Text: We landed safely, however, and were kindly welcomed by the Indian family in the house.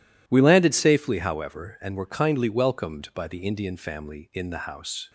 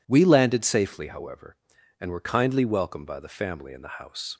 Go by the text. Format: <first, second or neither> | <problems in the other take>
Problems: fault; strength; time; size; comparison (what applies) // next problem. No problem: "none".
first | skips "Indian"; at 3.3 s